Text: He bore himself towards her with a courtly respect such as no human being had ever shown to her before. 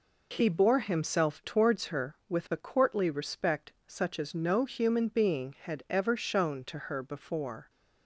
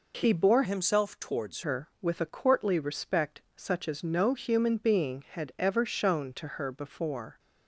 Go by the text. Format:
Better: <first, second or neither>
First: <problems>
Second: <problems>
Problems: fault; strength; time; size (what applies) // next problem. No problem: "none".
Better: first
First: pauses between "respect" and "such"; slight; at 3.7 s; 0.16 s long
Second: changes voice from "himself" to "towards"; from 0.6 to 1.6 s; 1.0 s long // pauses between "respect" and "such"; slight; at 3.4 s; 0.16 s long